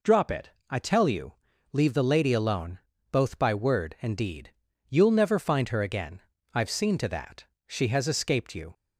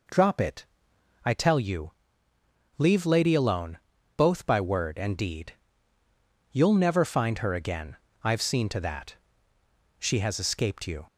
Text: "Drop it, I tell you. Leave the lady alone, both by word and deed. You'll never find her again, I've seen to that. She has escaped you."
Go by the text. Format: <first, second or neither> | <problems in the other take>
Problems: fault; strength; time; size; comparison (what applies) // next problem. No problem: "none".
first | skips "the"; at 3.0 s